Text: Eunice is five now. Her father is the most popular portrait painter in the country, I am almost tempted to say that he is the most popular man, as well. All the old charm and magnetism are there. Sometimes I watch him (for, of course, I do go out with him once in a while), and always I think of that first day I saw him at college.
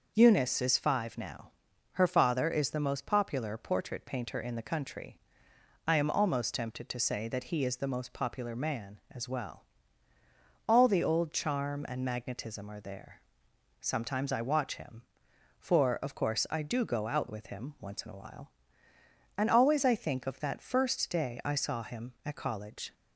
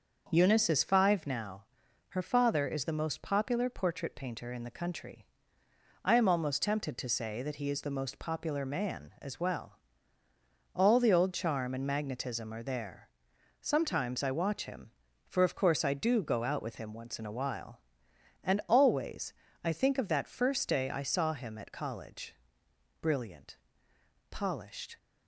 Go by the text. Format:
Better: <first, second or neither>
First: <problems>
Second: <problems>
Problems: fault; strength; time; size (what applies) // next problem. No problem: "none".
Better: first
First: none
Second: starts louder than the rest; noticeable; until 1.3 s; 6 dB // pauses between "always" and "I"; slight; at 19.3 s; 0.32 s long // goes on to say "Brilliant polished"; strong; from 23.0 s on; 1.9 s long